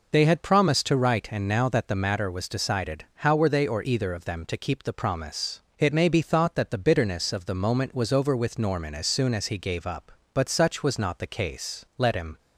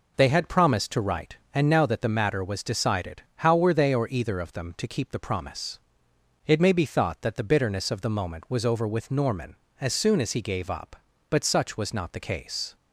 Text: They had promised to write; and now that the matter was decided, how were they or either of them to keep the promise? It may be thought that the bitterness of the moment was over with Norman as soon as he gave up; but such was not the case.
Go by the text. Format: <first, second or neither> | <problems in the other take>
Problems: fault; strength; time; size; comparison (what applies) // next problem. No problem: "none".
second | goes on to say "Let him"; slight; from 11.9 s on; 0.40 s long